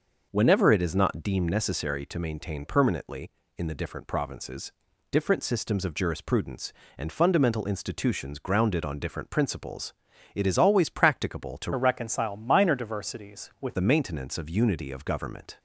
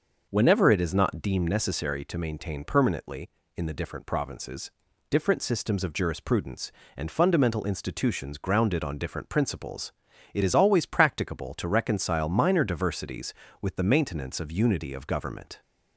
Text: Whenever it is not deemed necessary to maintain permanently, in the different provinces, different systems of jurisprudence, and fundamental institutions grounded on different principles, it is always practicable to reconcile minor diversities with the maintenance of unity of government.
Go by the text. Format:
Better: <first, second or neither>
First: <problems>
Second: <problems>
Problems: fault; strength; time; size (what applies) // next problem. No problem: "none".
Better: second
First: changes voice from "reconcile" to "with"; from 11.7 to 13.7 s; 2.0 s long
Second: none